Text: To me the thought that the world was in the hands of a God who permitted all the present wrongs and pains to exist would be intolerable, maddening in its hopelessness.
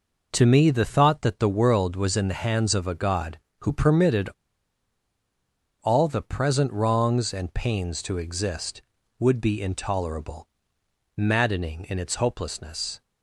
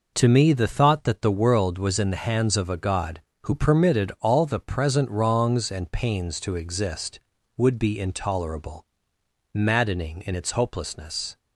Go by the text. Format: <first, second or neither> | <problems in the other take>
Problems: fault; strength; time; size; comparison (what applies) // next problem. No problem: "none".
second | pauses between "permitted" and "all"; strong; at 4.2 s; 1.5 s long